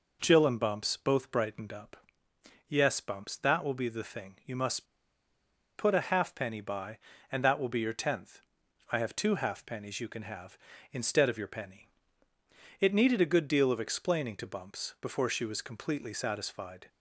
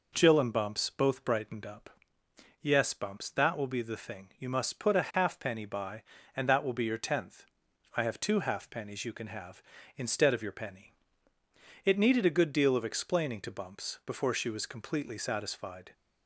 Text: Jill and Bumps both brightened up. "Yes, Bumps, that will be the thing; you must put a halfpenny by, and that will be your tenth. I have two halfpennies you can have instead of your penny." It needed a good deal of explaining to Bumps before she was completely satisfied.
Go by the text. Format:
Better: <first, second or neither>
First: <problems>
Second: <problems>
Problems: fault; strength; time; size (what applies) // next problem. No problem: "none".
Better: second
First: pauses between "must" and "put"; noticeable; at 4.8 s; 0.93 s long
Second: none